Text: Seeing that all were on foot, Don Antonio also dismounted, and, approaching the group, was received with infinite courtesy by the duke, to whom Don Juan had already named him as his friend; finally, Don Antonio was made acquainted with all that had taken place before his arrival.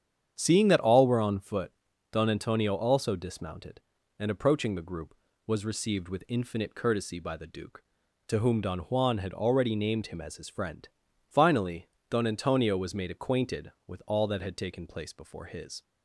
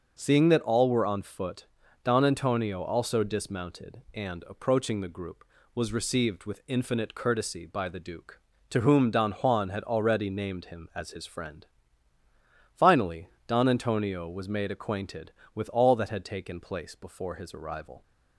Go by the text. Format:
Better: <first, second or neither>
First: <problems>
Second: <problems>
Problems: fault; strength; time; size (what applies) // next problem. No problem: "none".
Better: second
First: starts louder than the rest; strong; until 1.3 s; 8.5 dB // stops before "arrival"; at 15.8 s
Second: starts louder than the rest; until 1.1 s; 6.5 dB